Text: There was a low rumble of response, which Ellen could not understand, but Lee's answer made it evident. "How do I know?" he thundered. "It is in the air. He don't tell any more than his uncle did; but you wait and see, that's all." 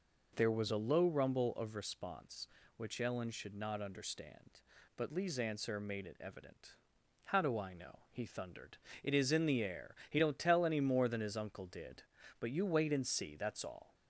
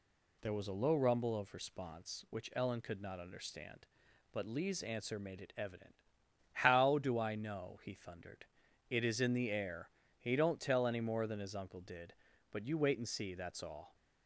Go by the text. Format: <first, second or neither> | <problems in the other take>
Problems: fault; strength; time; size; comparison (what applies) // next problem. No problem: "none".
second | says "should" for "could"; at 3.2 s